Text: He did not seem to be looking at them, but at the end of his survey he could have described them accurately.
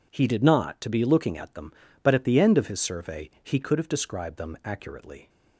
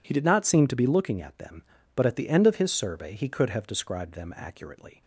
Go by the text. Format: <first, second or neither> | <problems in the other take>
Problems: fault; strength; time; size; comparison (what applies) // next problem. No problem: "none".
second | skips "seem"; at 0.8 s